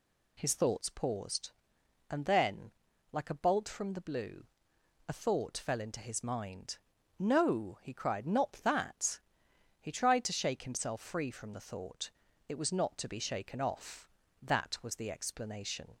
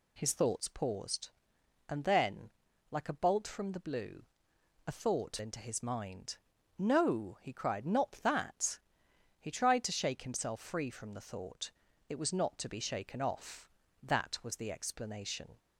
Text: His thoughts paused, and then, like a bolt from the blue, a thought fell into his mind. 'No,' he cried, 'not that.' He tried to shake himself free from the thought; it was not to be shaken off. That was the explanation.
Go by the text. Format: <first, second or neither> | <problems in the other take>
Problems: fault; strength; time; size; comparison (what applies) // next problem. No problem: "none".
first | skips "fell"; at 5.3 s